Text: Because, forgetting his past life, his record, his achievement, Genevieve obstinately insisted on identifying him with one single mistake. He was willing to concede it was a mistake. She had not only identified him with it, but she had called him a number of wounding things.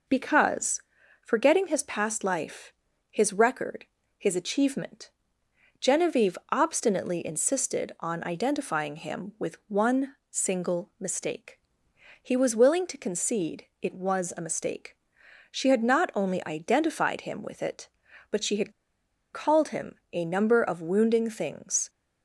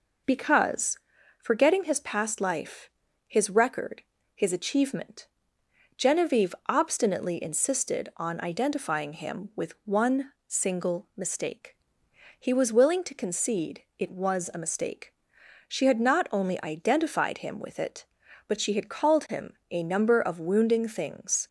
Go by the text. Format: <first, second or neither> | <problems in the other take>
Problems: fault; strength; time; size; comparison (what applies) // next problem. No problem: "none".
second | pauses between "one" and "single"; slight; at 10.1 s; 0.16 s long; slight in the second // pauses between "had" and "called"; noticeable; at 18.7 s; 0.61 s long // pauses between "him" and "a"; slight; at 19.9 s; 0.18 s long; slight in the second